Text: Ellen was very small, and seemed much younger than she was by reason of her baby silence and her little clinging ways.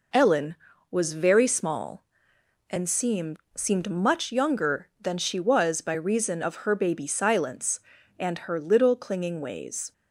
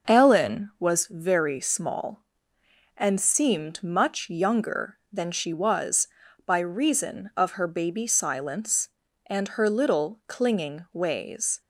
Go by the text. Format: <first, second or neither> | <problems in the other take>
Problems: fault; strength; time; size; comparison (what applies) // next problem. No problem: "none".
second | says "seemed" twice; at 3.5 s